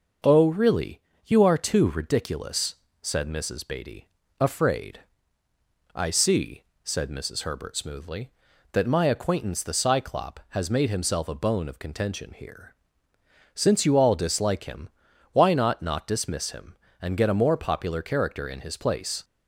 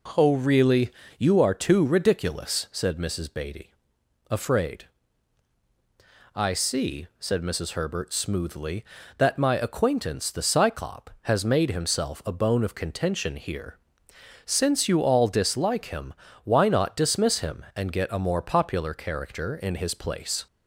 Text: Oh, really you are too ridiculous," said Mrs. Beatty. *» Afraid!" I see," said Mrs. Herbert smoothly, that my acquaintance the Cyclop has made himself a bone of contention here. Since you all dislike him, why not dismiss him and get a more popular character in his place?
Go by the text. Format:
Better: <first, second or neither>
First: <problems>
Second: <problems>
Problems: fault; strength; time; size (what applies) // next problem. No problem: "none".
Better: second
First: starts louder than the rest; until 1.4 s; 6 dB // pauses between "really" and "you"; slight; at 0.9 s; 0.24 s long // says "not" twice; at 15.8 s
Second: pauses between "really" and "you"; slight; at 0.9 s; 0.28 s long